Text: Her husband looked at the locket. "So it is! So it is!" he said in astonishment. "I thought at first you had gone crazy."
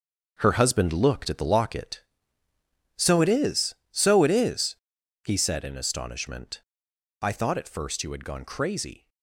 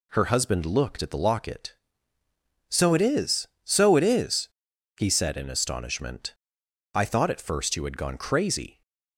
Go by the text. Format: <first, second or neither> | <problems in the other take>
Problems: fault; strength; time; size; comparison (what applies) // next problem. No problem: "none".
second | gets quieter; strong; throughout; 10.5 dB